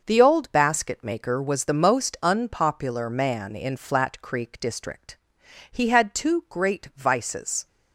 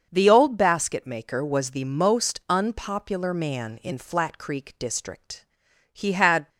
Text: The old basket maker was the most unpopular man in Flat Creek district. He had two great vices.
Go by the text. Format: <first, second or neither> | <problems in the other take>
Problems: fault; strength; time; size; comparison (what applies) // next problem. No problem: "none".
first | starts louder than the rest; until 1.1 s; 6.5 dB // stops before "two great vices"; at 6.4 s